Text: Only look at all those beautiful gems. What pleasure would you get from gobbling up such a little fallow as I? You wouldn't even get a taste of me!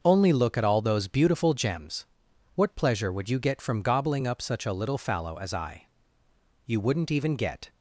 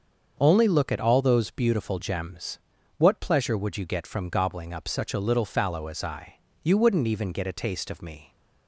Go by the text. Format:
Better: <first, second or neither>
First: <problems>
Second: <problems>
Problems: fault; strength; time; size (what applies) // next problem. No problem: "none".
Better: second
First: starts louder than the rest; until 1.0 s; 6.5 dB // stops before "a taste of me"; at 7.6 s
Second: starts louder than the rest; until 1.4 s; 6.5 dB